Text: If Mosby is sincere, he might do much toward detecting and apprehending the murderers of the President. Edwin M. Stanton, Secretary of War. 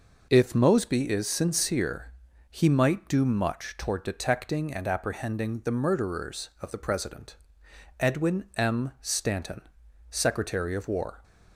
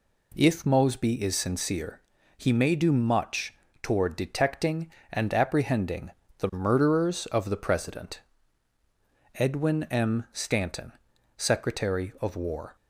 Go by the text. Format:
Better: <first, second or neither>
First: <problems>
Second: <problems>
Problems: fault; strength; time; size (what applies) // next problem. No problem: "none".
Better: first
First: none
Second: says "may" for "might"; at 2.5 s // pauses between "much" and "toward"; slight; at 3.5 s; 0.30 s long // pauses between "apprehending" and "the"; slight; at 6.1 s; 0.28 s long